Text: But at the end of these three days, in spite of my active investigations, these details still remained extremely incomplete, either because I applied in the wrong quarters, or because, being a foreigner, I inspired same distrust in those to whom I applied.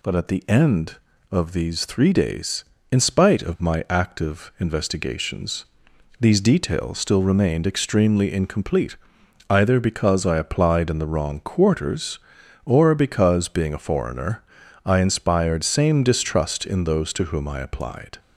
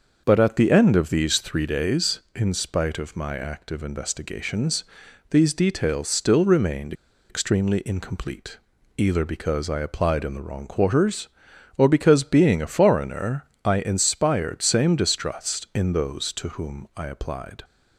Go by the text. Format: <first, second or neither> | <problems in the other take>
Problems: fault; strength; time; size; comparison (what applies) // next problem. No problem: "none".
first | starts louder than the rest; noticeable; until 1.2 s; 6 dB // pauses between "remained" and "extremely"; at 6.9 s; 0.37 s long